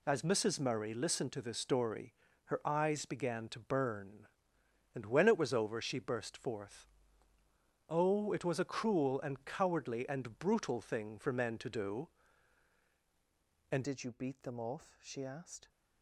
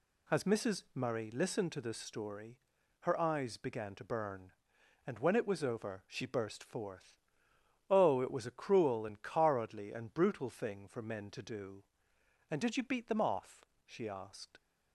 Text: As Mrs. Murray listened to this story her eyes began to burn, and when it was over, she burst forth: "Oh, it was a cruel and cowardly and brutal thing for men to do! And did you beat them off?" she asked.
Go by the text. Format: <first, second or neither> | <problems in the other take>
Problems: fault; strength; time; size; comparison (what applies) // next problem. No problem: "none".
second | pauses between "story" and "her"; slight; at 2.1 s; 0.34 s long; also in the second // changes voice at "did"; from 13.8 s on; 1.8 s long